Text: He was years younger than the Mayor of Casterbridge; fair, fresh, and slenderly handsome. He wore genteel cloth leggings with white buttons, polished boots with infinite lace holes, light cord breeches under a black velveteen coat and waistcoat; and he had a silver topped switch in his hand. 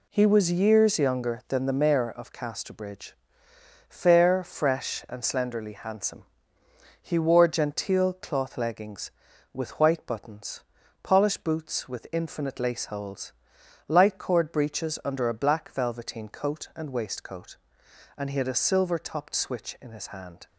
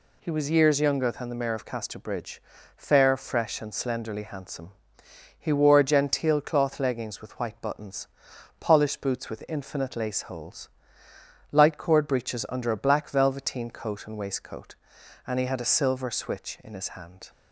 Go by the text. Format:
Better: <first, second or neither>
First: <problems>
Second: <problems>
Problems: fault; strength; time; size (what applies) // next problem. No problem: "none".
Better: first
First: none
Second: skips "topped"; at 16.0 s